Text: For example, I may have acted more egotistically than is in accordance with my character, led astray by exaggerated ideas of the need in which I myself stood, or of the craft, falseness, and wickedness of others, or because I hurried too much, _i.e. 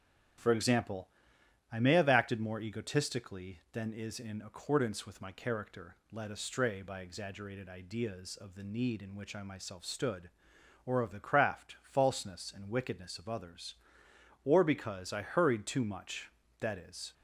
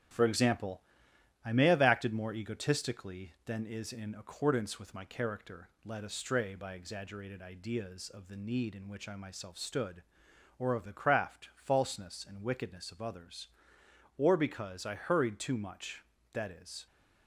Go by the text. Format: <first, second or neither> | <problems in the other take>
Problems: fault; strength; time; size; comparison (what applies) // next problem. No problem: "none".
first | gets quieter; throughout; 3.5 dB // starts louder than the rest; strong; until 1.7 s; 10 dB; strong in the first